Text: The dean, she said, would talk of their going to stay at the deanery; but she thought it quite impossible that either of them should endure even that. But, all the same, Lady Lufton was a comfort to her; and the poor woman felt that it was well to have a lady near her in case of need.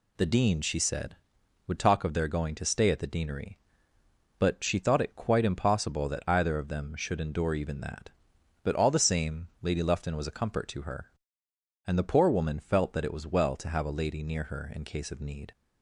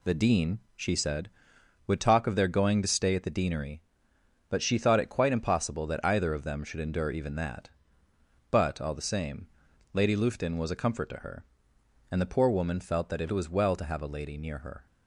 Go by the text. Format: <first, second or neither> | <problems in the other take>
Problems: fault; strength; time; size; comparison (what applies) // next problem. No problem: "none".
first | stops before "in case of need"; at 14.8 s